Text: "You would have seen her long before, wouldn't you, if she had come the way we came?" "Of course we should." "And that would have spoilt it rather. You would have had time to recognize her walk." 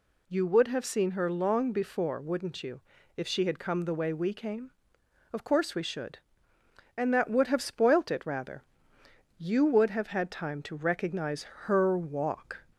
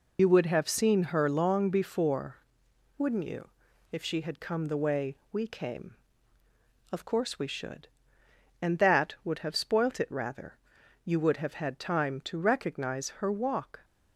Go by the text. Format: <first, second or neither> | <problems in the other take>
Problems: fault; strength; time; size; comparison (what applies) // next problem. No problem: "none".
first | loses the start of "You"; at 0.1 s; 50 ms // pauses between "way" and "we"; slight; at 5.1 s; 0.16 s long // pauses between "recognize" and "her"; slight; at 13.0 s; 0.16 s long; slight in the first